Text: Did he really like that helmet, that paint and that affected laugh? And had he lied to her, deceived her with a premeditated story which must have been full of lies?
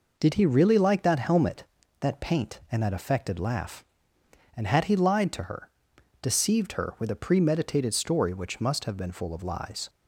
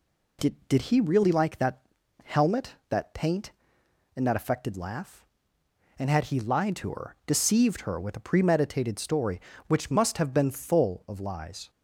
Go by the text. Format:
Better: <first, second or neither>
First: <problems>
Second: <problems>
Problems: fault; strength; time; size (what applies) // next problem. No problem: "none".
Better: first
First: none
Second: says "Did" twice; at 0.6 s // pauses between "that" and "helmet"; at 1.8 s; 0.42 s long